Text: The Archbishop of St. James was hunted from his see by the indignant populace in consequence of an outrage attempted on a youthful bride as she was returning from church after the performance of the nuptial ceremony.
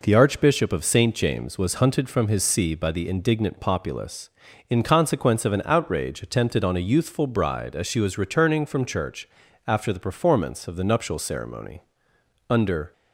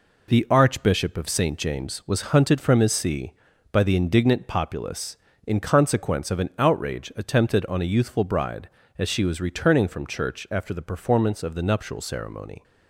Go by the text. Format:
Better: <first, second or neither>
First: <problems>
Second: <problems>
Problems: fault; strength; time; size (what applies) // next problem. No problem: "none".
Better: second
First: pauses between "church" and "after"; at 9.2 s; 0.40 s long // goes on to say "Under"; slight; from 12.4 s on; 0.42 s long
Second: none